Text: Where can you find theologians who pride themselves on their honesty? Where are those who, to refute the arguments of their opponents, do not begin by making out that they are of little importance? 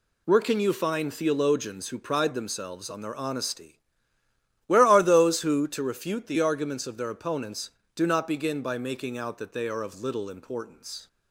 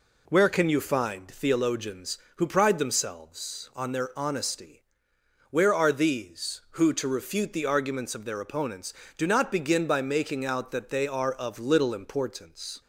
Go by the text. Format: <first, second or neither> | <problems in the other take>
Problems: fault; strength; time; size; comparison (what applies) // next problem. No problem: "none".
first | says "these" for "those"; at 5.9 s